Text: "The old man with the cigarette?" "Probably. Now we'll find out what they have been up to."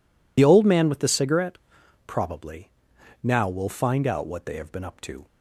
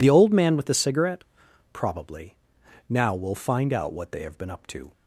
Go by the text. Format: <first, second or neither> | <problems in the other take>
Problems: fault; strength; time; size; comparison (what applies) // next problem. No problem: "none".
second | loses the start of "The"; at 0.3 s; 30 ms